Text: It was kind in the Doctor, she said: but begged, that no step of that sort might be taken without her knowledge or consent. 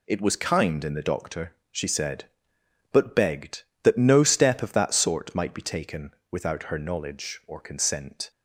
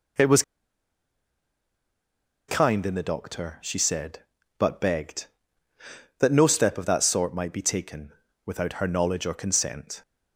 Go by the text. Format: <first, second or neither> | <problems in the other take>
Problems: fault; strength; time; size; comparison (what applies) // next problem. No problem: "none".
first | pauses between "was" and "kind"; strong; at 0.4 s; 2.0 s long // pauses between "taken" and "without"; slight; at 8.1 s; 0.32 s long; slight in the first